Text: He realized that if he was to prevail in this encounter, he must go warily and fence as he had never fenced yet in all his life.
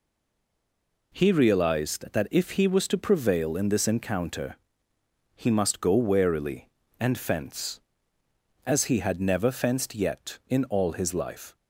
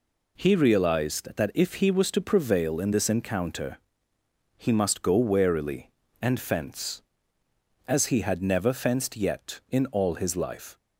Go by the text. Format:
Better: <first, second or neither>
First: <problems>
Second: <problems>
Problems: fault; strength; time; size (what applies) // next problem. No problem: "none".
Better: second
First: stays silent before the first word; until 1.1 s; 1.1 s long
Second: none